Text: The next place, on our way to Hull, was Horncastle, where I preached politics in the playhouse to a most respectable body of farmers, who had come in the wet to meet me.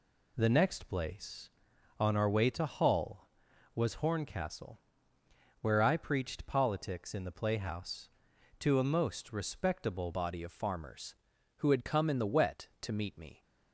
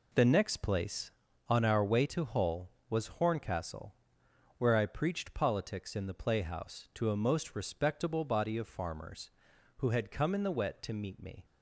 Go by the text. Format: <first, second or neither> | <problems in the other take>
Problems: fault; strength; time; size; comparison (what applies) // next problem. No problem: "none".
second | changes voice at "body"; from 10.1 s on; 3.3 s long